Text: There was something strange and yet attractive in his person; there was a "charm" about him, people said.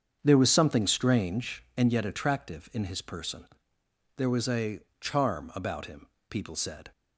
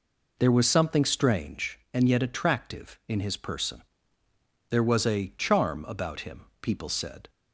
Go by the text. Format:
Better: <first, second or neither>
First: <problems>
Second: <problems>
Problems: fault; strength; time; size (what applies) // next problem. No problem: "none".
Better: second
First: starts louder than the rest; strong; until 1.9 s; 7.5 dB // pauses between "a" and "charm"; slight; at 4.8 s; 0.18 s long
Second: none